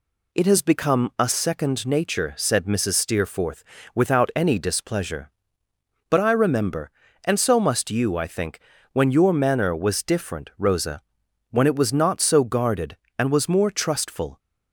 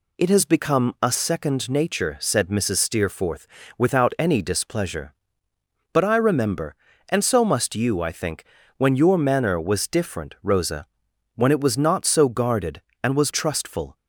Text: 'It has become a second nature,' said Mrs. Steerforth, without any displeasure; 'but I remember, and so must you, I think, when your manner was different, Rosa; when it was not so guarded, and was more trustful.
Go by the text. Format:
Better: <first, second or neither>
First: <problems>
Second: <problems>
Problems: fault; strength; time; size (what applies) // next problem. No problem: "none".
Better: first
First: none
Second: skips "more"; at 13.3 s